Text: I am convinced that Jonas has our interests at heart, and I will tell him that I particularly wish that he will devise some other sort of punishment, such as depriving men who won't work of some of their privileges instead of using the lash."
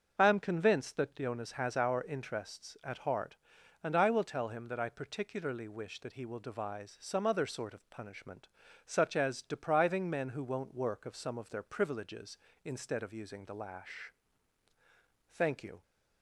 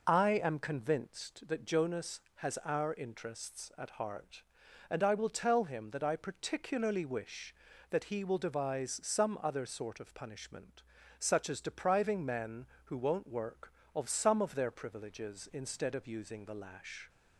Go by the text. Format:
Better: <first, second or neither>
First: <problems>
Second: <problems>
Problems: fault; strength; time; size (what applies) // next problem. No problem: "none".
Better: second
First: starts louder than the rest; until 1.1 s; 6.5 dB // goes on to say "Thank you"; from 15.3 s on; 0.50 s long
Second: none